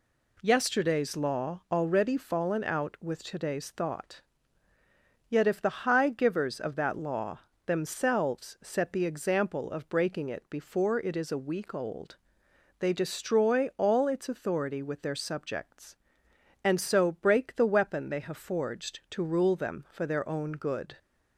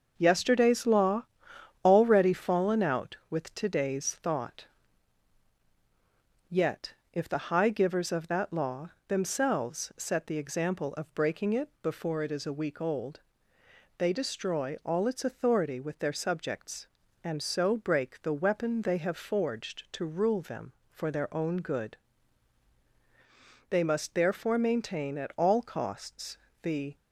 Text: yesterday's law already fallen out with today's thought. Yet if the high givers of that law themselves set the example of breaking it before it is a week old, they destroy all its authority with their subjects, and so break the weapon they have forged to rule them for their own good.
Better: first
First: pauses between "law" and "themselves"; slight; at 7.3 s; 0.26 s long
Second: starts louder than the rest; until 1.1 s; 6 dB // pauses between "law" and "already"; noticeable; at 1.2 s; 0.60 s long // pauses between "Yet" and "if"; slight; at 6.9 s; 0.20 s long // pauses between "law" and "themselves"; slight; at 8.8 s; 0.18 s long // goes on to say "They must therefore maintain at all costs the"; strong; from 23.6 s on; 3.2 s long

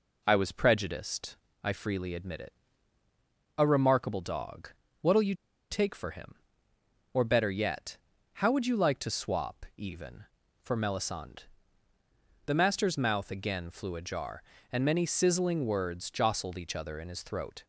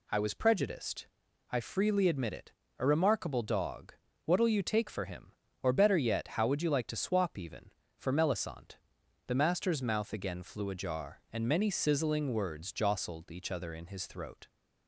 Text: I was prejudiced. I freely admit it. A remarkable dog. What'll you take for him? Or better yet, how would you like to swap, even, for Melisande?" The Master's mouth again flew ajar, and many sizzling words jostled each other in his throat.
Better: second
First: pauses between "you" and "take"; slight; at 5.3 s; 0.36 s long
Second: none

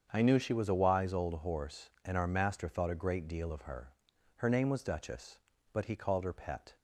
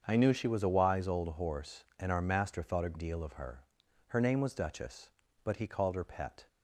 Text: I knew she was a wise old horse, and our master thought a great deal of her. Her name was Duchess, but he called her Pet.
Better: first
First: starts louder than the rest; strong; until 1.1 s; 7 dB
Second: starts louder than the rest; until 1.0 s; 7 dB // skips "great"; at 2.9 s

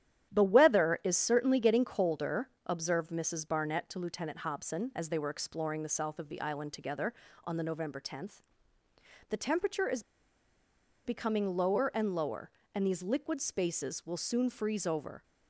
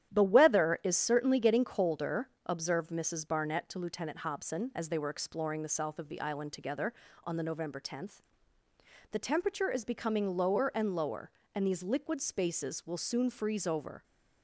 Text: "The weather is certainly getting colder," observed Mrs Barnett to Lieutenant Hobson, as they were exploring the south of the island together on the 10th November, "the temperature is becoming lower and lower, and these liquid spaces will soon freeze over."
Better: second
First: starts louder than the rest; strong; until 1.3 s; 11 dB // pauses between "is" and "becoming"; at 10.0 s; 1.0 s long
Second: starts louder than the rest; strong; until 1.1 s; 11 dB

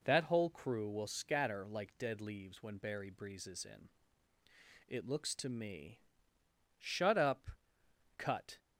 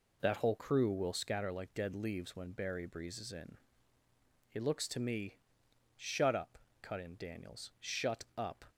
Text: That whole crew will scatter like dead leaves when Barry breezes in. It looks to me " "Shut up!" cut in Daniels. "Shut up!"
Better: second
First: stops before "in Daniels Shut up"; at 8.5 s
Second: none

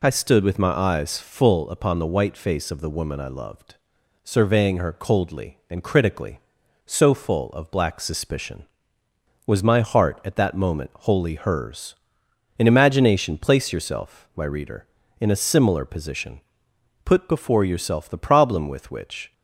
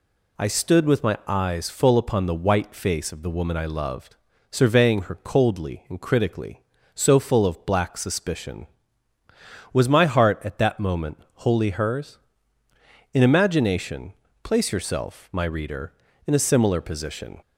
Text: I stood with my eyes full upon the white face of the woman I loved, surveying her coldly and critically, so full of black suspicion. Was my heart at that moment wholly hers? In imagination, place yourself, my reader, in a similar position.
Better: second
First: goes on to say "Put before yourself the problem with which"; strong; from 17.0 s on; 2.2 s long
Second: none

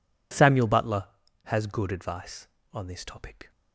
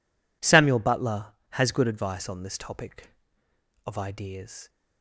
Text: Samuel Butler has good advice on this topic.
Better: first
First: none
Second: goes on to say "Of ideas"; noticeable; from 3.8 s on; 0.82 s long

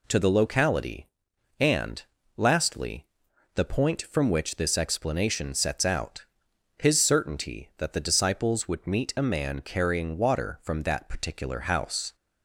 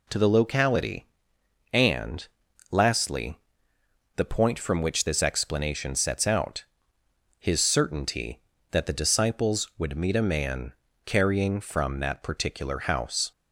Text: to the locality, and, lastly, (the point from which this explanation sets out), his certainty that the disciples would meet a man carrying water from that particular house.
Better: first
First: none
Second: pauses between "man" and "carrying"; slight; at 10.7 s; 0.32 s long // skips "water"; at 11.5 s

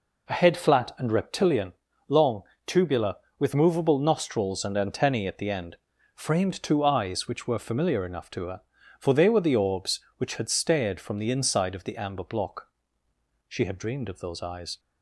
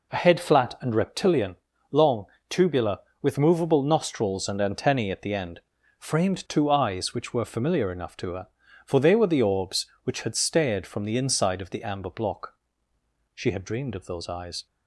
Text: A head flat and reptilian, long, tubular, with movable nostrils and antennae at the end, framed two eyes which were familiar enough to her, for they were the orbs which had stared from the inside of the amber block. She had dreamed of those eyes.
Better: neither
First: none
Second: none

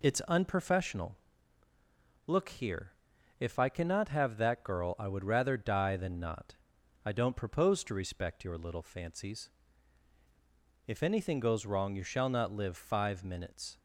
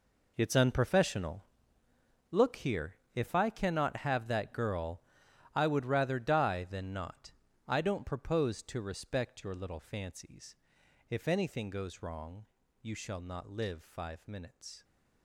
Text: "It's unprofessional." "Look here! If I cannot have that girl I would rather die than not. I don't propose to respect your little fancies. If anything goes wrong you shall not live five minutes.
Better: first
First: none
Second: gets quieter; strong; throughout; 13.5 dB // pauses between "girl" and "I"; noticeable; at 5.0 s; 0.50 s long // pauses between "wrong" and "you"; slight; at 12.4 s; 0.36 s long

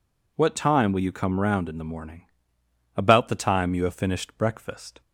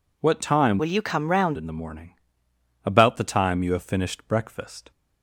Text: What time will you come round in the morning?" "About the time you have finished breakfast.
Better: first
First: none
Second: changes voice from "will" to "round"; from 0.7 to 1.5 s; 0.8 s long

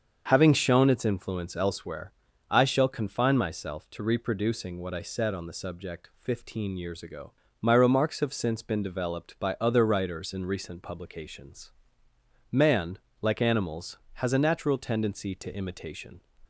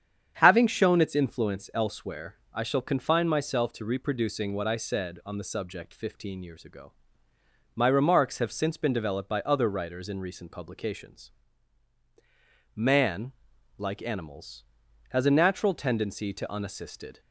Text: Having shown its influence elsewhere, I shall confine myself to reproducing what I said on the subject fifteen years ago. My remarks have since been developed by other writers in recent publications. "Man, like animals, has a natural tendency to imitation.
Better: first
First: starts louder than the rest; until 1.3 s; 6.5 dB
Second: starts louder than the rest; strong; until 1.4 s; 8 dB // says "unassisted" for "imitation"; at 16.5 s

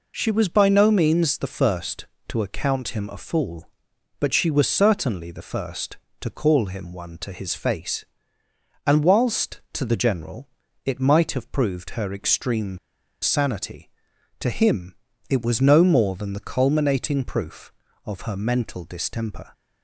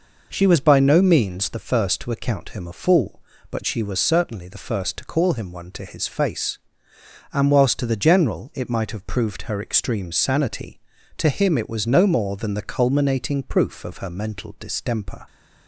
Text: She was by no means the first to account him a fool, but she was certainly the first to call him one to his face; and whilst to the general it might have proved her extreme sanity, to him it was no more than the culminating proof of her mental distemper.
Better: second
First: pauses between "general" and "it"; slight; at 10.4 s; 0.36 s long // pauses between "extreme" and "sanity"; at 12.7 s; 0.44 s long // pauses between "him" and "it"; slight; at 14.9 s; 0.34 s long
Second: none

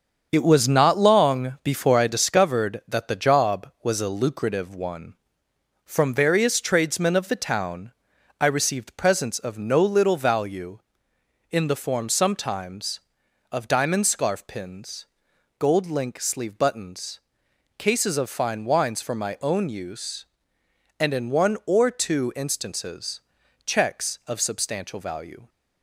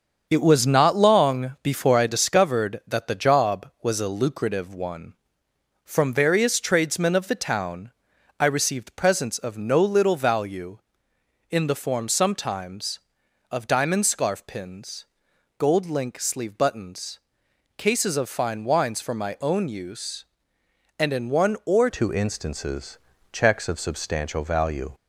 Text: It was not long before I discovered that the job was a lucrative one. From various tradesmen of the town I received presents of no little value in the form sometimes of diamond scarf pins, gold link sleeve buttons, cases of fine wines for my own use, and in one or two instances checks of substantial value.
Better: first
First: starts louder than the rest; until 1.3 s; 7 dB // pauses between "town" and "I"; noticeable; at 7.9 s; 0.46 s long // pauses between "instances" and "checks"; at 23.2 s; 0.44 s long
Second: starts louder than the rest; until 1.3 s; 7 dB // pauses between "town" and "I"; noticeable; at 7.9 s; 0.46 s long // changes voice at "two"; from 21.8 s on; 3.1 s long // pauses between "instances" and "checks"; slight; at 22.9 s; 0.34 s long

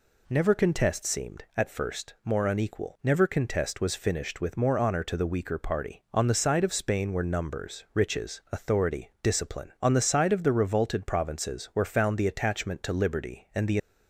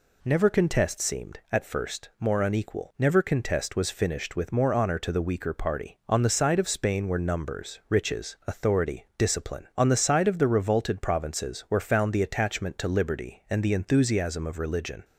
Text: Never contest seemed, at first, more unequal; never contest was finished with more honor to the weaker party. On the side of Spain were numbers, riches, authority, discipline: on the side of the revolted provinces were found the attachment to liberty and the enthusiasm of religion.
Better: second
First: stops before "enthusiasm of religion"; at 13.7 s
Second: none

